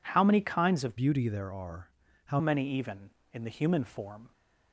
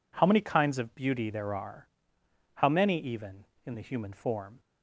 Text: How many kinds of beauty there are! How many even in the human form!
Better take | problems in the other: second | changes voice from "beauty" to "How"; from 0.9 to 2.3 s; 1.4 s long

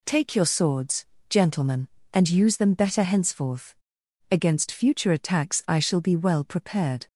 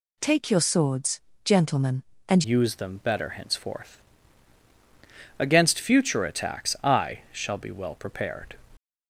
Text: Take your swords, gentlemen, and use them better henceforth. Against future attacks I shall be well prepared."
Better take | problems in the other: first | changes voice at "use"; from 2.4 s on; 6.1 s long

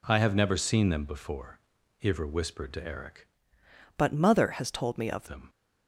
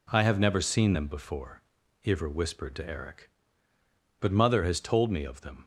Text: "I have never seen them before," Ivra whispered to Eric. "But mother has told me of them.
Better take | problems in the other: second | changes voice from "But" to "of"; from 3.9 to 5.2 s; 1.3 s long

